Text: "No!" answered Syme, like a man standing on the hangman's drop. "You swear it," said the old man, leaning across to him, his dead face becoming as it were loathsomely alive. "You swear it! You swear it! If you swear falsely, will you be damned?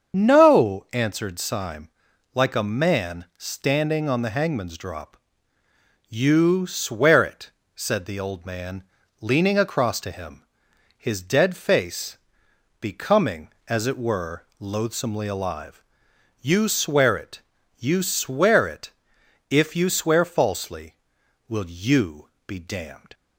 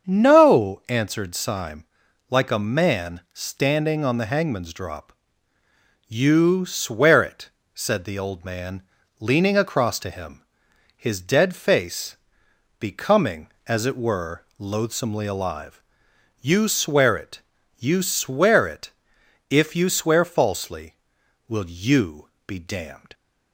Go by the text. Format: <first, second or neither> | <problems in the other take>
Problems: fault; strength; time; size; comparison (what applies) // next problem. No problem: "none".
second | loses the start of "No"; at 0.1 s; 40 ms // starts louder than the rest; until 1.2 s; 7 dB; also in the second // pauses between "face" and "becoming"; noticeable; at 12.1 s; 0.60 s long; noticeable in the second // pauses between "you" and "be"; slight; at 22.2 s; 0.16 s long; slight in the second